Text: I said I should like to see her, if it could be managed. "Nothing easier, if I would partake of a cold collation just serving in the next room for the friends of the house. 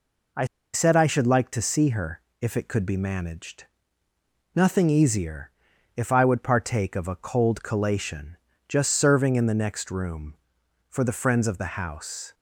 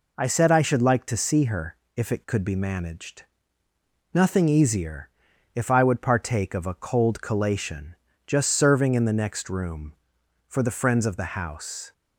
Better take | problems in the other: second | pauses between "I" and "said"; slight; at 0.4 s; 0.28 s long // pauses between "collation" and "just"; slight; at 8.3 s; 0.32 s long; slight in the second

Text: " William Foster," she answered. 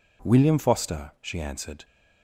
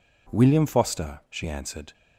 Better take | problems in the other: neither | none

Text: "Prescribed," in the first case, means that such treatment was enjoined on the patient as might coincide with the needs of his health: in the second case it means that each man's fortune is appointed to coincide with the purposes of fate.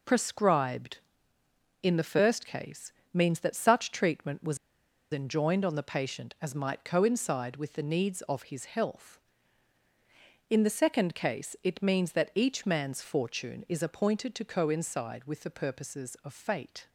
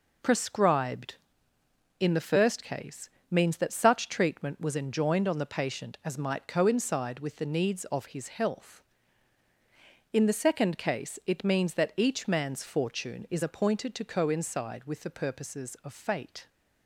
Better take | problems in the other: second | pauses between "was" and "enjoined"; noticeable; at 4.5 s; 0.54 s long

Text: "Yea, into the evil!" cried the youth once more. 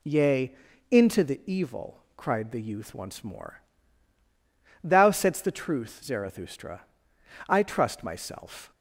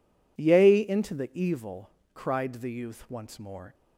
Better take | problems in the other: second | goes on to say "Thou saidst the truth Zarathustra I trust myself"; strong; from 4.8 s on; 3.9 s long

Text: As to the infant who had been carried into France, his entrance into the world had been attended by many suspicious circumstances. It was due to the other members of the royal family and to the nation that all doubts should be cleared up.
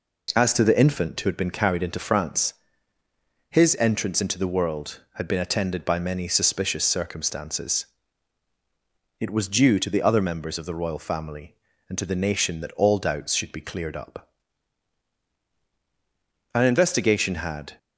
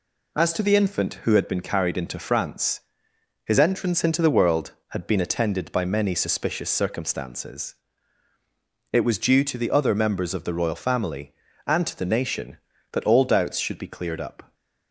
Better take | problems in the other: second | goes on to say "An investigation had"; noticeable; from 16.5 s on; 1.2 s long

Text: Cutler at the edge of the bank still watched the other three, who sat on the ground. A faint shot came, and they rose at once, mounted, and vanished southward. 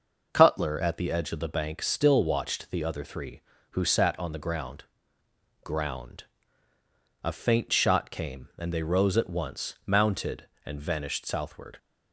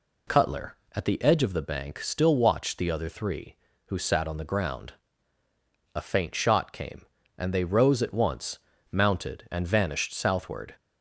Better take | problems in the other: second | says "ground" twice; at 5.6 s

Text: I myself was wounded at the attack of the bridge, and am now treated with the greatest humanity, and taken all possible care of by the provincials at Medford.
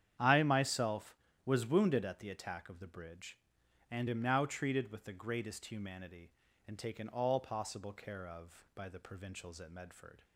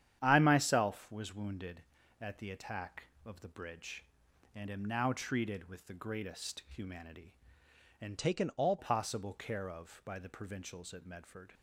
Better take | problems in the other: first | starts louder than the rest; strong; until 1.2 s; 10 dB; strong in the first // changes voice from "taken" to "all"; from 8.1 to 8.7 s; 0.6 s long

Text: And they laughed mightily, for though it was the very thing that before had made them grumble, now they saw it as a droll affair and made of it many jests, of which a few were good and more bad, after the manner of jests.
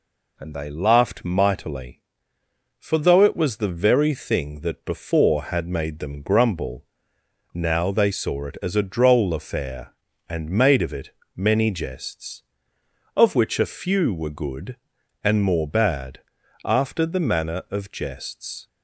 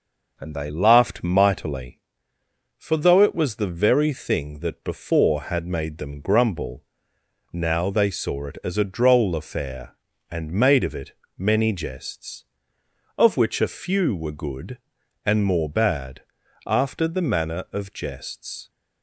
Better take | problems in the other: first | starts louder than the rest; noticeable; until 2.1 s; 5.5 dB // pauses between "it" and "many"; slight; at 11.1 s; 0.24 s long; slight in the first

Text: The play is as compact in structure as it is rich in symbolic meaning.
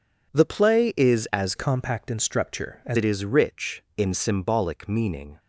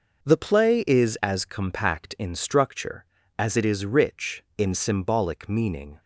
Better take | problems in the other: second | changes voice from "compact" to "as"; from 1.5 to 2.9 s; 1.4 s long

